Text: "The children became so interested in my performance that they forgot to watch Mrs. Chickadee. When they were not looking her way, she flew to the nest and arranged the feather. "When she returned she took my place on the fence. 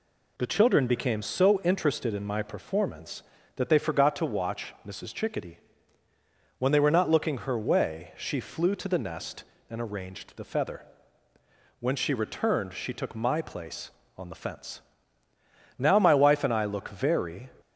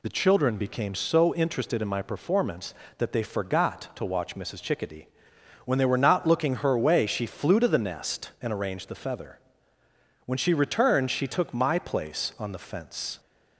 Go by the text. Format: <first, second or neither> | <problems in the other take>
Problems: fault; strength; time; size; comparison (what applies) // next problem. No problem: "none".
second | goes on to say "Now my wife and I look very"; strong; from 15.7 s on; 1.7 s long